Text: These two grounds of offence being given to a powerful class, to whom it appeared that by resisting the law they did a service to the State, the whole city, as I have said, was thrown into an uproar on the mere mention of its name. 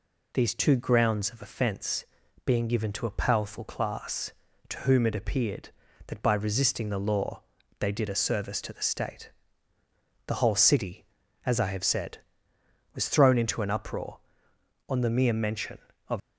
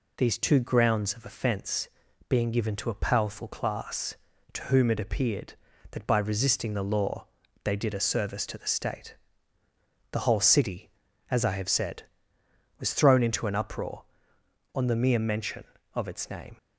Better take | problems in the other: second | pauses between "offence" and "being"; at 2.0 s; 0.40 s long; also in the second // pauses between "law" and "they"; at 7.4 s; 0.38 s long; also in the second // stops before "its name"; at 16.2 s

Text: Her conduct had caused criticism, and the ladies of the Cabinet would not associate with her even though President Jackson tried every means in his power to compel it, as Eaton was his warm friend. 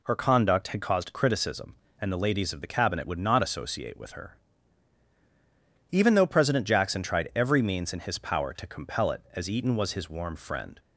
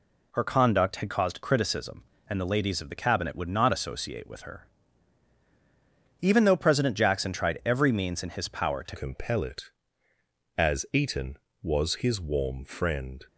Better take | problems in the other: first | pauses between "her" and "even"; strong; at 4.6 s; 1.5 s long; strong in the first // changes voice at "compel"; from 8.9 s on; 4.3 s long

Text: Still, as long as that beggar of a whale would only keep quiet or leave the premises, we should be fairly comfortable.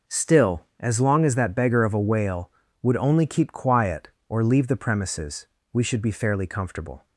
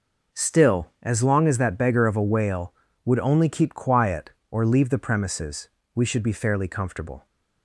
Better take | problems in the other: neither | none

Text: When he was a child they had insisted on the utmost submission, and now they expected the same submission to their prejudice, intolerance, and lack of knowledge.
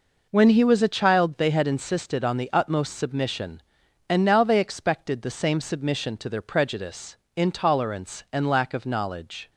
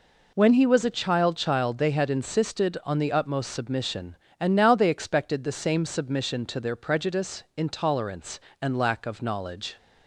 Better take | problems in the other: first | says "child" twice; at 1.3 s

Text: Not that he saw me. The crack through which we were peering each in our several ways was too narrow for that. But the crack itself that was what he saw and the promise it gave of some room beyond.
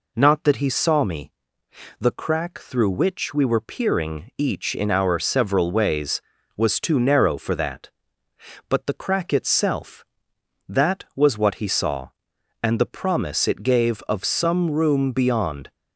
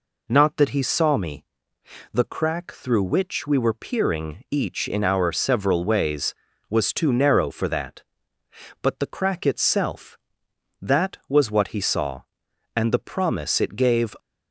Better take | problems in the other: first | stops before "of some room beyond"; at 14.1 s

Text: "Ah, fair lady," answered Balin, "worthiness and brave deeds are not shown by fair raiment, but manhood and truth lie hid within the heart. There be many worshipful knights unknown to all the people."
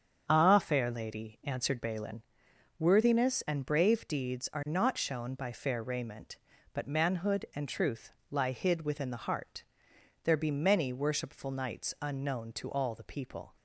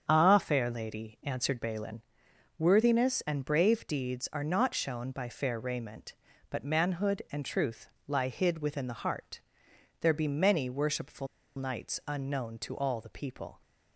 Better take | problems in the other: first | starts louder than the rest; strong; until 1.0 s; 7 dB; strong in the first // pauses between "truth" and "lie"; slight; at 7.8 s; 0.18 s long; slight in the first // pauses between "worshipful" and "knights"; slight; at 11.2 s; 0.29 s long

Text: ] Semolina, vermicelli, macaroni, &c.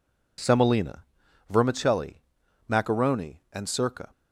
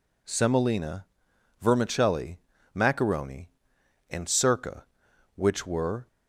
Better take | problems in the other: first | goes on to say "which were"; noticeable; from 5.3 s on; 0.72 s long

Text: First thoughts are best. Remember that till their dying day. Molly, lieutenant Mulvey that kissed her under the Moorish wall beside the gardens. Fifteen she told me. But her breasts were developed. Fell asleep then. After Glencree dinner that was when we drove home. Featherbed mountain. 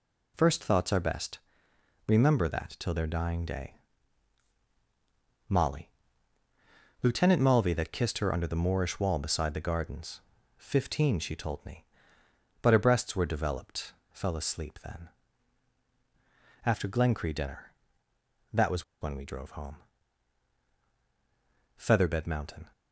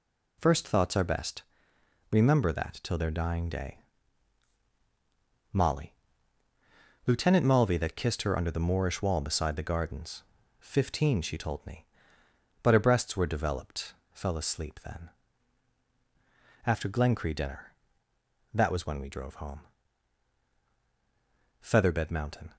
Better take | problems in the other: second | pauses between "was" and "when"; slight; at 18.8 s; 0.17 s long

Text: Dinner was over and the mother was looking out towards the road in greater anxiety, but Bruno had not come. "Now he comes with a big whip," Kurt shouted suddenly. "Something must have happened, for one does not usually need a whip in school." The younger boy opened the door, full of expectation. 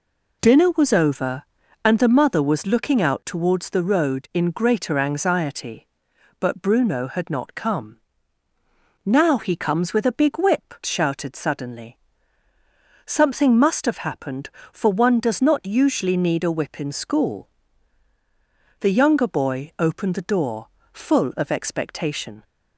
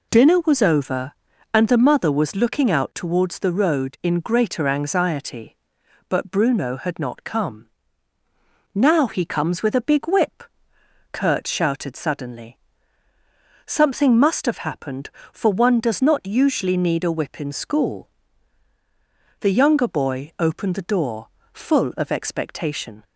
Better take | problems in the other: second | skips "Kurt"; at 10.8 s

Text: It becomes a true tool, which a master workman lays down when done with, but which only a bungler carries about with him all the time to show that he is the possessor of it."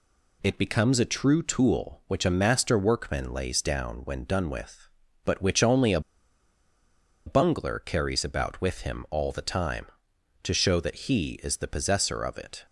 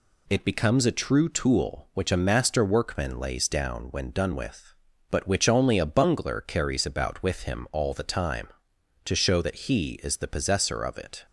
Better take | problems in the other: second | pauses between "a" and "bungler"; strong; at 5.9 s; 1.2 s long

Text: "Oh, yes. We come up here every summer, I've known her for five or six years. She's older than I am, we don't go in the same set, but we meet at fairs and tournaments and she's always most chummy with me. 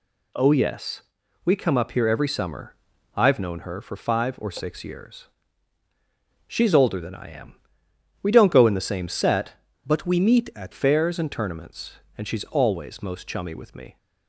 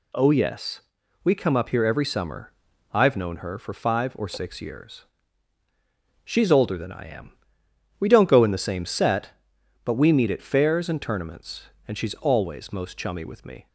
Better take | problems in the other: second | changes voice from "but" to "at"; from 9.8 to 10.7 s; 0.9 s long

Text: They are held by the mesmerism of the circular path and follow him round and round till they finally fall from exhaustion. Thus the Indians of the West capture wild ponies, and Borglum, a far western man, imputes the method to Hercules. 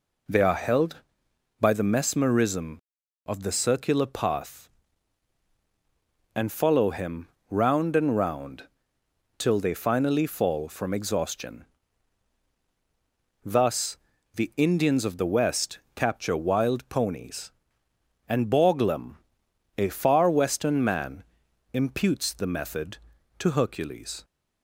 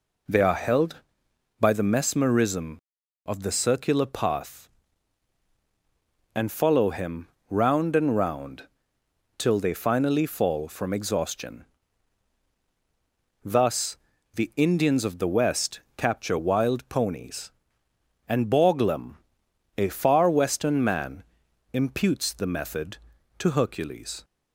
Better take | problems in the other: neither | pauses between "him" and "round"; slight; the same in both // pauses between "round" and "till"; noticeable; the same in both // pauses between "Thus" and "the"; the same in both // pauses between "West" and "capture"; slight; the same in both

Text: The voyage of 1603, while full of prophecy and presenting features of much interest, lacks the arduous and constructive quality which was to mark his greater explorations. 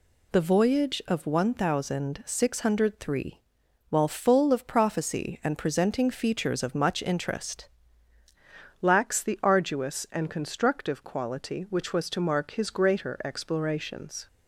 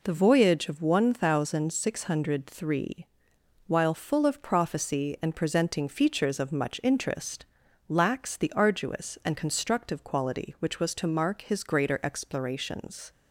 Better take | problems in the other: second | changes voice at "lacks"; from 8.8 s on; 5.4 s long

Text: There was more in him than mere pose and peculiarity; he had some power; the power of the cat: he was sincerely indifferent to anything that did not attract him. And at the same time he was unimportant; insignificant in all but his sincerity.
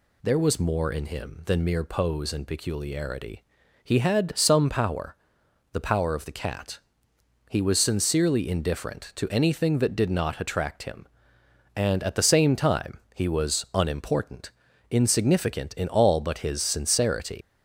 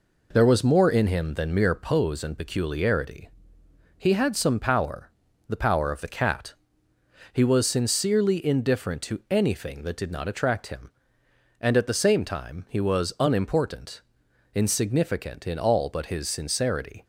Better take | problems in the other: second | pauses between "time" and "he"; slight; at 12.9 s; 0.16 s long // leaves "sincerity" unfinished; at 17.4 s; 135 ms

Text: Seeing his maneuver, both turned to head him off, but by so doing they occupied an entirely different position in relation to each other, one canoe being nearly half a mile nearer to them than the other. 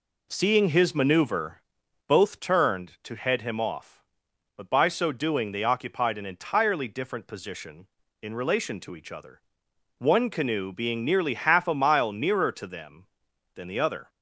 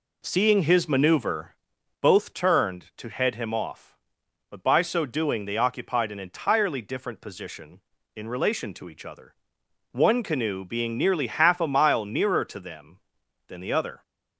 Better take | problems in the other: neither | none

